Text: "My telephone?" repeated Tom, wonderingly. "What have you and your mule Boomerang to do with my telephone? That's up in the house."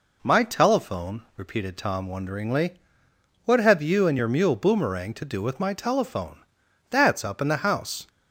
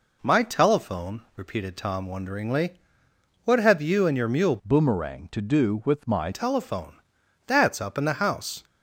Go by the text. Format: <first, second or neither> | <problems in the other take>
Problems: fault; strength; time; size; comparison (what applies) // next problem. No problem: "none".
first | changes voice from "Boomerang" to "my"; from 4.6 to 6.3 s; 1.7 s long